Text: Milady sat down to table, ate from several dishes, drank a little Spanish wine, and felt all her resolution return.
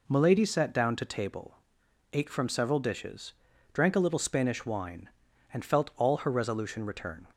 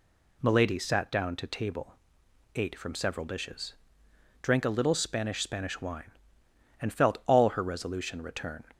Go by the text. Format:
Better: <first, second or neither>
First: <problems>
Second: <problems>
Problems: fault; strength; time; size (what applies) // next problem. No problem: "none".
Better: first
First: none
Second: says "Spanish" twice; at 5.4 s